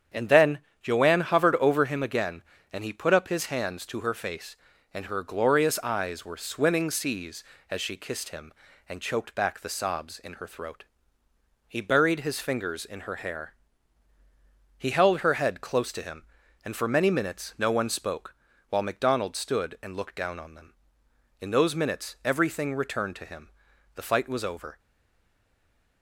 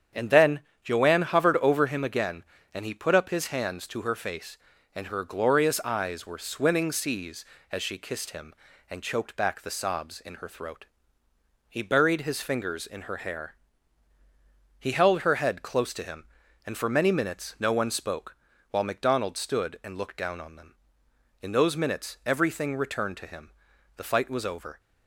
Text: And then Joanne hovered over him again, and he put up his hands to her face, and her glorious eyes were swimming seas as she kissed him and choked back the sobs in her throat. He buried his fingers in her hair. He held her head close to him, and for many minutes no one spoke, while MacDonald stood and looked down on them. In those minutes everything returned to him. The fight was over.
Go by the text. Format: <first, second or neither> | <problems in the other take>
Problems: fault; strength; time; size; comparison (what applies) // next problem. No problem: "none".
second | starts louder than the rest; strong; until 1.3 s; 8.5 dB; strong in the second // pauses between "then" and "Joanne"; slight; at 0.5 s; 0.24 s long; slight in the second // stays silent after the last word; noticeable; from 24.7 s on; 1.3 s long